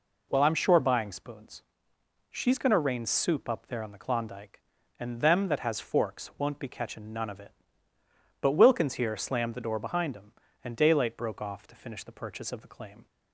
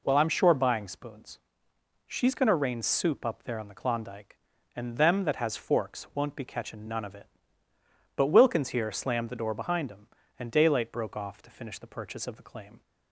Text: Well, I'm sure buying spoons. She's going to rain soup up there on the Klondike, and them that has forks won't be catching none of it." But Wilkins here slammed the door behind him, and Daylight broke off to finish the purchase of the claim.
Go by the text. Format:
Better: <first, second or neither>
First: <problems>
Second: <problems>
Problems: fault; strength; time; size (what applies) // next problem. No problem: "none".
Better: neither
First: none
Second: none